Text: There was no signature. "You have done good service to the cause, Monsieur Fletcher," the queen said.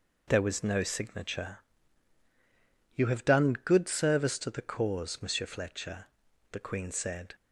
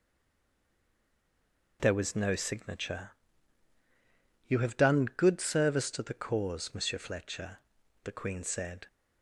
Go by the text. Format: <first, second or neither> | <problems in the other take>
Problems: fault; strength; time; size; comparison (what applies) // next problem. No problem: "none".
first | stays silent before the first word; noticeable; until 1.7 s; 1.7 s long